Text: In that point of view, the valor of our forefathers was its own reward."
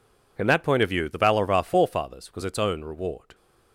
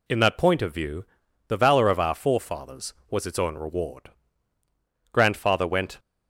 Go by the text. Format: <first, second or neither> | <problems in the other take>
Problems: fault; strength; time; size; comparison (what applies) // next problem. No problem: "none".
first | goes on to say "Grandfather went"; noticeable; from 5.1 s on; 0.86 s long